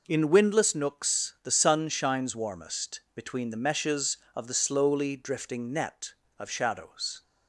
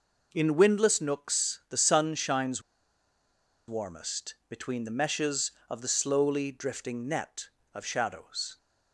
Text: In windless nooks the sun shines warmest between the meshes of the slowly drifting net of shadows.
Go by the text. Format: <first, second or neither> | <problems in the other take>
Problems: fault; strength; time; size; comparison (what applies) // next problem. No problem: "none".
first | pauses between "shines" and "warmest"; at 2.6 s; 1.0 s long // pauses between "warmest" and "between"; slight; at 4.3 s; 0.16 s long; slight in the first